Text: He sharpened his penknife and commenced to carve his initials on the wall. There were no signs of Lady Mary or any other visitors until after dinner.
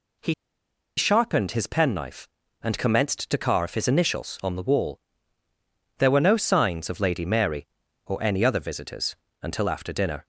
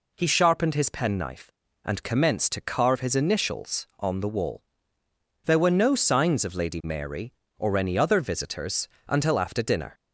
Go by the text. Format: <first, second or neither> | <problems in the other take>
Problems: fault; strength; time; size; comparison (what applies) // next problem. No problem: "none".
second | pauses between "He" and "sharpened"; noticeable; at 0.3 s; 0.64 s long // pauses between "visitors" and "until"; slight; at 9.1 s; 0.26 s long; slight in the second